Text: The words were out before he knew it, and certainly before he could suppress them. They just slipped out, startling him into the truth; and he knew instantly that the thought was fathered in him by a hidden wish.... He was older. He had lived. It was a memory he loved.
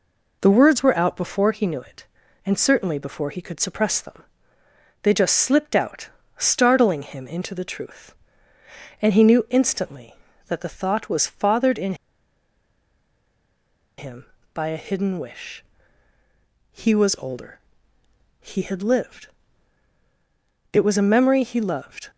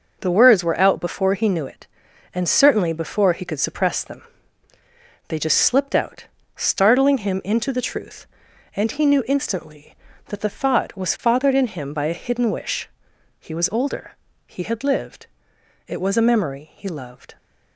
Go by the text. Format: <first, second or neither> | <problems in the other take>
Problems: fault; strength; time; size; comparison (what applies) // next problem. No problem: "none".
second | pauses between "in" and "him"; strong; at 11.9 s; 2.0 s long